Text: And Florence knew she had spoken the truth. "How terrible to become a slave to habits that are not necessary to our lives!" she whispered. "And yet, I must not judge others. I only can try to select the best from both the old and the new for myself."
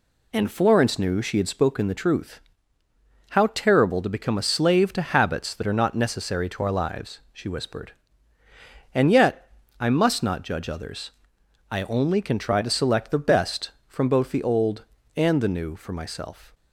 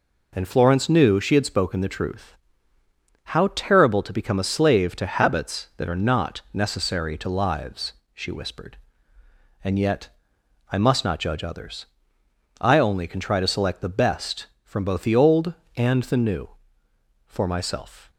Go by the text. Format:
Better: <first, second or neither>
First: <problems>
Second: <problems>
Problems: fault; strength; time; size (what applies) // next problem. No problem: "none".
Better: first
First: none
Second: skips "our"; at 7.2 s